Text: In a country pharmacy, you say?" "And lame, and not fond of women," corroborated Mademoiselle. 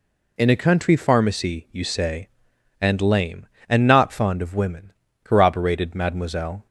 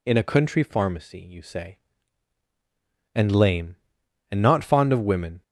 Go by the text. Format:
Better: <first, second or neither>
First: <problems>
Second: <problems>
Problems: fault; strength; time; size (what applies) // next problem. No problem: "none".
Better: first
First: none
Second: stops before "corroborated Mademoiselle"; at 5.4 s